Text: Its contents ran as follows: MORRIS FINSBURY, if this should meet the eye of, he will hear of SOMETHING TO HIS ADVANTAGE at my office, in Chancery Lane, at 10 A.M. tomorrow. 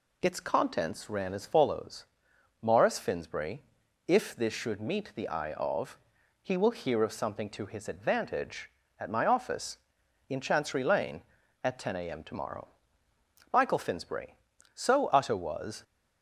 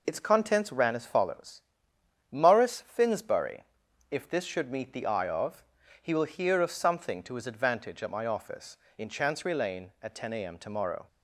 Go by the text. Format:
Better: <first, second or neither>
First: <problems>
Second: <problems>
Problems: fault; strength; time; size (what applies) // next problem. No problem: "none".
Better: second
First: goes on to say "MICHAEL FINSBURY So utter was"; strong; from 13.5 s on; 2.3 s long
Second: none